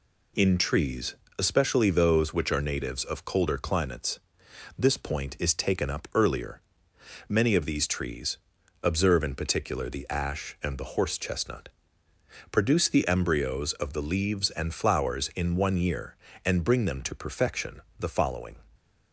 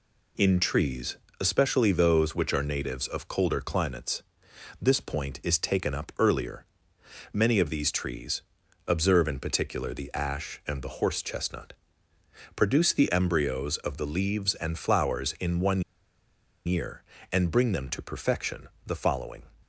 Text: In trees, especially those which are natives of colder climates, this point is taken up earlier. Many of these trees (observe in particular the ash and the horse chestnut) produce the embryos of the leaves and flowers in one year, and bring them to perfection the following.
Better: first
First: pauses between "perfection" and "the"; slight; at 17.8 s; 0.18 s long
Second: pauses between "one" and "year"; noticeable; at 15.8 s; 0.85 s long // pauses between "perfection" and "the"; slight; at 18.6 s; 0.18 s long

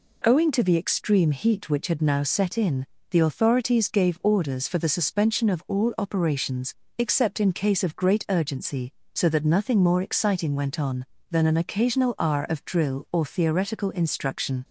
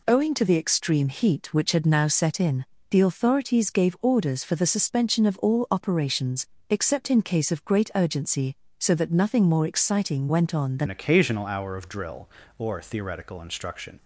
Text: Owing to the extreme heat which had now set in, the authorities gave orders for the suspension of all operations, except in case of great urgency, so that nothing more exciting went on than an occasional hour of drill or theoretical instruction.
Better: first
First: none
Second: changes voice at "an"; from 10.8 s on; 3.1 s long

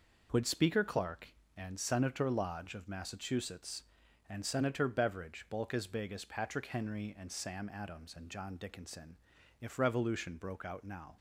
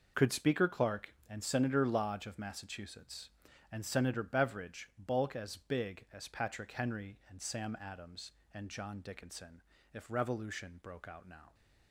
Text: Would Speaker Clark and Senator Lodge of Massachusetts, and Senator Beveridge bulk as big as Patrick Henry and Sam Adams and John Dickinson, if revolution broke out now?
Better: first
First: none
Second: says "Could" for "Would"; at 0.1 s

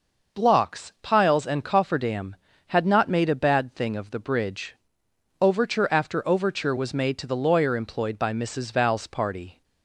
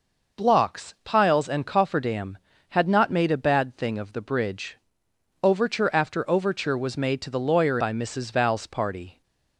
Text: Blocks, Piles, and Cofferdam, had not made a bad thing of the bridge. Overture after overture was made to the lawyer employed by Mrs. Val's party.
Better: first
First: none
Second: skips "employed"; at 7.7 s

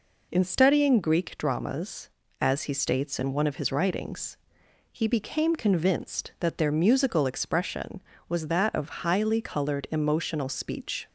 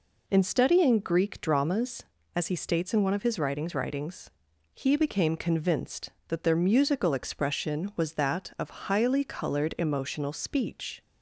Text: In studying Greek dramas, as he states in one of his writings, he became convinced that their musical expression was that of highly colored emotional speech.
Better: first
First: none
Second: says "writings" twice; at 3.7 s

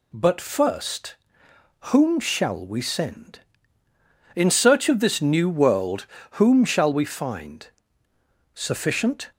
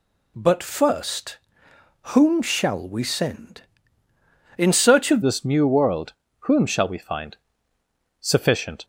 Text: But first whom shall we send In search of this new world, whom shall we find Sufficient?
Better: first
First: pauses between "first" and "whom"; noticeable; at 1.1 s; 0.76 s long // pauses between "find" and "Sufficient"; noticeable; at 7.6 s; 0.88 s long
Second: pauses between "first" and "whom"; noticeable; at 1.3 s; 0.76 s long // changes voice at "this"; from 5.2 s on; 3.6 s long // pauses between "find" and "Sufficient"; noticeable; at 7.3 s; 0.86 s long

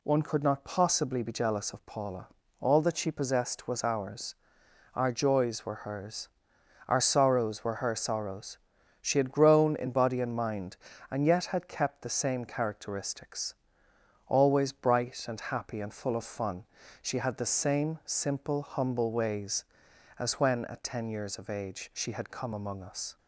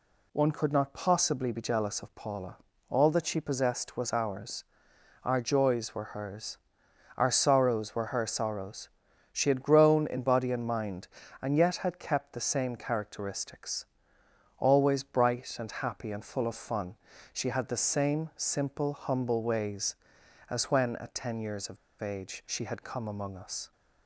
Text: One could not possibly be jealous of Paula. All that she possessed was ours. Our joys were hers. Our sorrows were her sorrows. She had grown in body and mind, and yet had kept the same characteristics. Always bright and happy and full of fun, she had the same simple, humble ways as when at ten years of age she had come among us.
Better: first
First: none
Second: pauses between "of" and "age"; slight; at 21.7 s; 0.24 s long

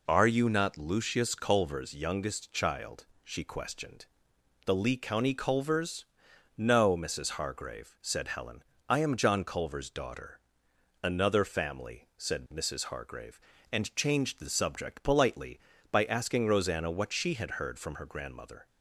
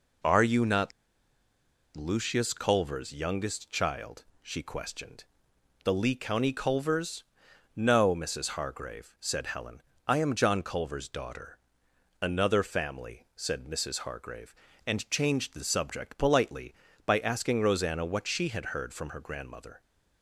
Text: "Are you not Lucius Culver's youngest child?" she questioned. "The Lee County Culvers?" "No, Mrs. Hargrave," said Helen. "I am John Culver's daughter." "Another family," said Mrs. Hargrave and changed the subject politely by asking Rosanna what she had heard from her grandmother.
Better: first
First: none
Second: pauses between "not" and "Lucius"; at 0.9 s; 1.0 s long

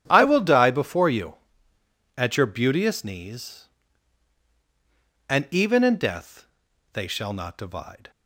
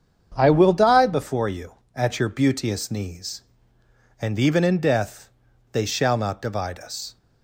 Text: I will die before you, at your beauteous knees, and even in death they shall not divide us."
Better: second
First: starts louder than the rest; strong; until 1.0 s; 10 dB // pauses between "death" and "they"; noticeable; at 6.4 s; 0.46 s long // stops before "us"; at 8.1 s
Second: starts louder than the rest; strong; until 1.3 s; 7.5 dB // pauses between "death" and "they"; at 5.2 s; 0.44 s long

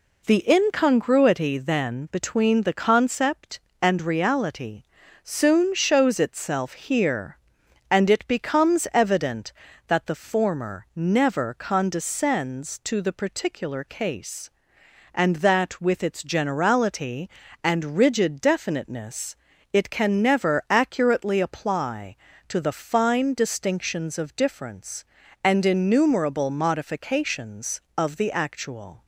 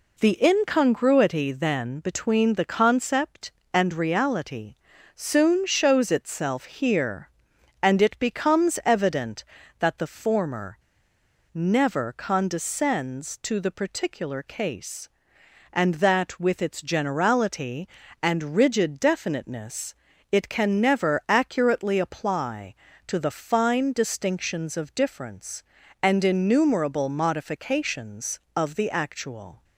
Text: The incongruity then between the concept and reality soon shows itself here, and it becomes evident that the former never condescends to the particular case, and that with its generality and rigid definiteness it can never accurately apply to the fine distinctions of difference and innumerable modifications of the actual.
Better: first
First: pauses between "reality" and "soon"; at 4.8 s; 0.40 s long // pauses between "definiteness" and "it"; at 19.3 s; 0.38 s long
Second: pauses between "reality" and "soon"; at 4.7 s; 0.40 s long // pauses between "former" and "never"; noticeable; at 10.7 s; 0.74 s long // pauses between "definiteness" and "it"; at 19.9 s; 0.38 s long

